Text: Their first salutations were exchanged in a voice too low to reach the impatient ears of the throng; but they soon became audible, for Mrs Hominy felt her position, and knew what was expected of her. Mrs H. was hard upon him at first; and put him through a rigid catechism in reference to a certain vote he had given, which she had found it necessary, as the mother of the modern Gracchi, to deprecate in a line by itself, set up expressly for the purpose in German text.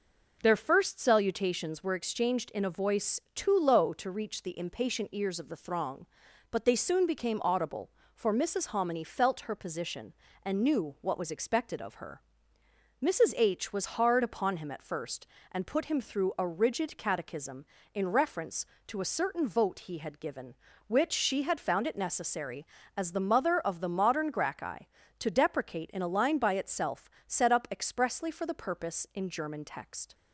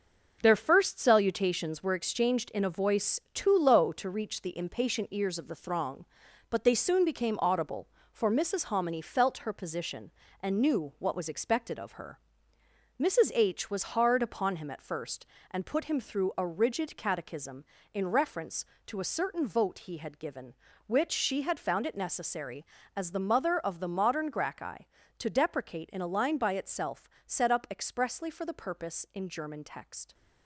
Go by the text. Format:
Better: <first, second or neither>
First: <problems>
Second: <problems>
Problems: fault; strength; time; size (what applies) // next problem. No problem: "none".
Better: first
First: none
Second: gets quieter; throughout; 7 dB